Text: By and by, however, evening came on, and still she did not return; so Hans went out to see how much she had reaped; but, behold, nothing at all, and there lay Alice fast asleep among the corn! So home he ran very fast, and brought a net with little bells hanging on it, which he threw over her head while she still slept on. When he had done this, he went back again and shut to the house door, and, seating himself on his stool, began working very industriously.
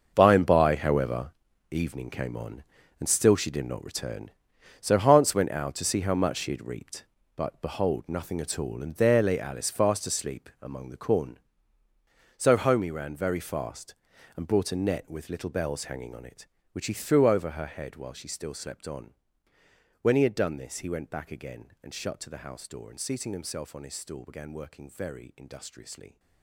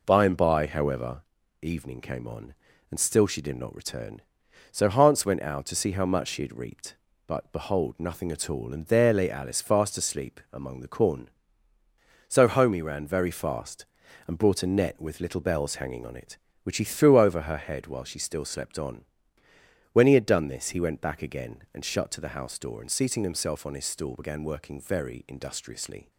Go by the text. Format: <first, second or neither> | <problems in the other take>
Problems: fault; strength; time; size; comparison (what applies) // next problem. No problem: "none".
second | gets quieter; strong; throughout; 13 dB